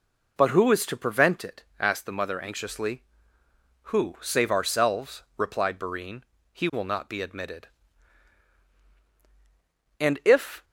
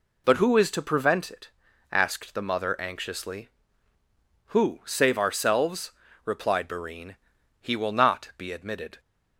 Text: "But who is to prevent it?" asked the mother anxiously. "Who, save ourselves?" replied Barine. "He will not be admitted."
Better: second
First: goes on to say "And if"; noticeable; from 9.9 s on; 0.64 s long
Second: none

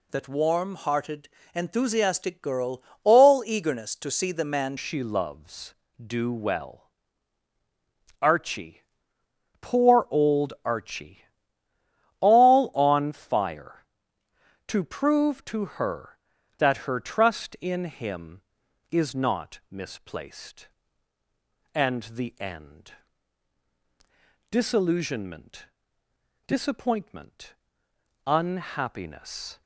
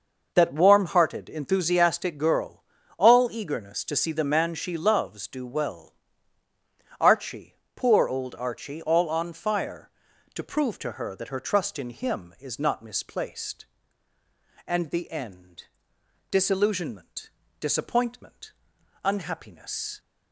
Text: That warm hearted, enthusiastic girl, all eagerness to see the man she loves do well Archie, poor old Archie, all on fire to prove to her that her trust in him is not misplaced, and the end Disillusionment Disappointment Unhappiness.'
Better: second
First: changes voice at "she"; from 4.7 s on; 24.9 s long // pauses between "well" and "Archie"; strong; at 6.8 s; 1.3 s long // pauses between "end" and "Disillusionment"; strong; at 22.9 s; 1.6 s long // pauses between "Disillusionment" and "Disappointment"; noticeable; at 25.6 s; 0.82 s long // pauses between "Disappointment" and "Unhappiness"; noticeable; at 27.5 s; 0.72 s long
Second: pauses between "well" and "Archie"; at 5.9 s; 1.0 s long // pauses between "end" and "Disillusionment"; noticeable; at 15.6 s; 0.66 s long // pauses between "Disillusionment" and "Disappointment"; slight; at 17.2 s; 0.30 s long // pauses between "Disappointment" and "Unhappiness"; noticeable; at 18.5 s; 0.52 s long

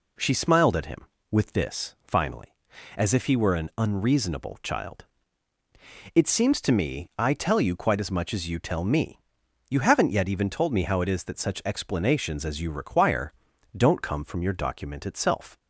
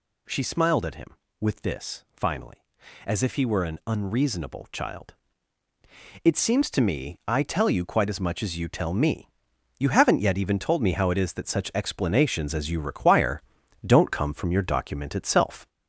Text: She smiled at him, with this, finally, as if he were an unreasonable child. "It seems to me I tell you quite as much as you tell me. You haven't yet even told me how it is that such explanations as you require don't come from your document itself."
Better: first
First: pauses between "require" and "don't"; at 13.3 s; 0.44 s long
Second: gets louder; noticeable; throughout; 4.5 dB // pauses between "require" and "don't"; at 13.4 s; 0.44 s long

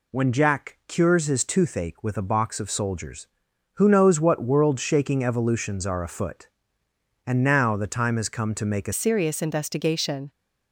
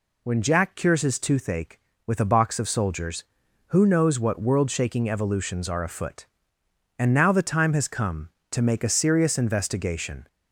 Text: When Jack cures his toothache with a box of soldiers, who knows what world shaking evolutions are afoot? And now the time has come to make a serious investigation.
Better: second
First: changes voice at "serious"; from 8.9 s on; 1.3 s long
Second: none

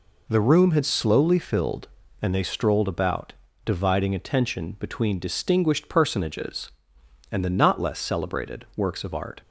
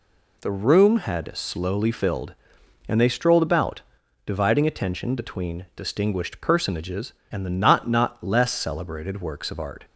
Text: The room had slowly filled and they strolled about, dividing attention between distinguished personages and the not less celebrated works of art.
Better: first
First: none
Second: says "not" twice; at 7.8 s

